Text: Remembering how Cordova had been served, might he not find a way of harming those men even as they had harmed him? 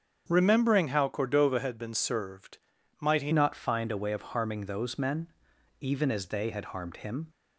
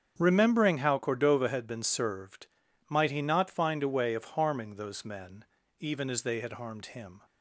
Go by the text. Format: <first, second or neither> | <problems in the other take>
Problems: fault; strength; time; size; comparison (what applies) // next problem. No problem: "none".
second | starts louder than the rest; strong; until 1.2 s; 7.5 dB; strong in the second // changes voice at "not"; from 3.3 s on; 3.9 s long // pauses between "men" and "even"; noticeable; at 5.2 s; 0.52 s long; slight in the second